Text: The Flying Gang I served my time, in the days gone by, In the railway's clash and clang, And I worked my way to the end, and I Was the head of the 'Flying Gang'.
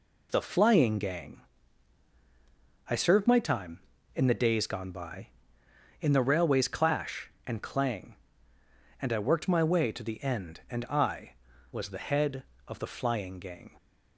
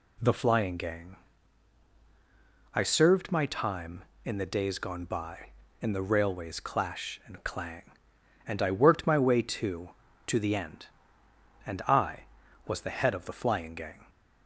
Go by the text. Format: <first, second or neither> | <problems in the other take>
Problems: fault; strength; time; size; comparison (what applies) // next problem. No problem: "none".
first | pauses between "Gang" and "I"; strong; at 1.1 s; 1.6 s long; strong in the first // says "to" twice; at 10.2 s